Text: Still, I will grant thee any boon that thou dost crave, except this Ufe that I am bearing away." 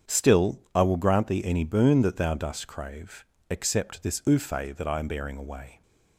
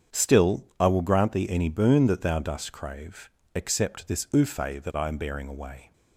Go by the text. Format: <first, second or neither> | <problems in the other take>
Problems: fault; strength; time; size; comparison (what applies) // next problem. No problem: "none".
neither | starts louder than the rest; strong; the same in both